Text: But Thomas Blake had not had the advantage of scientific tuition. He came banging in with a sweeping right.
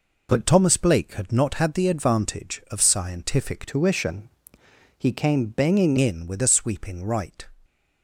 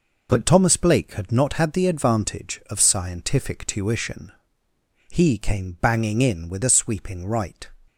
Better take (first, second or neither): second